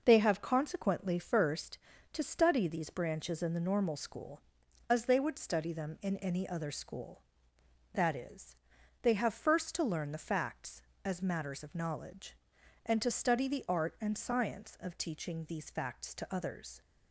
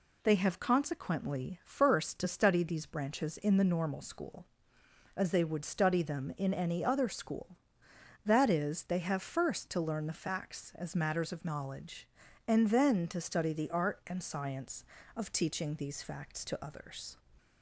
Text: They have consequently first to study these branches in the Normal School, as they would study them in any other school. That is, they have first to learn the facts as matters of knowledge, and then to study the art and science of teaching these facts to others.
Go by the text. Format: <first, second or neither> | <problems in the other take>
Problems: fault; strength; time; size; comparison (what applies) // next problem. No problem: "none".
second | skips "then"; at 13.0 s